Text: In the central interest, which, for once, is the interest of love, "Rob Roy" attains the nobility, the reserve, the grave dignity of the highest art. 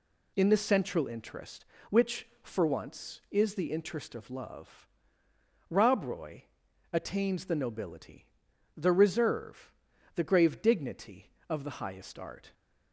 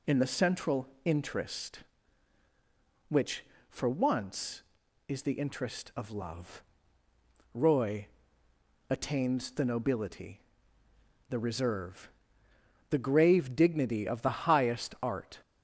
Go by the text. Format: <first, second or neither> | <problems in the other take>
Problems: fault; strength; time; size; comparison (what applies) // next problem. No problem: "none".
first | pauses between "central" and "interest"; slight; at 0.8 s; 0.20 s long // skips "Rob"; at 7.0 s // pauses between "Roy" and "attains"; noticeable; at 8.0 s; 0.84 s long; noticeable in the first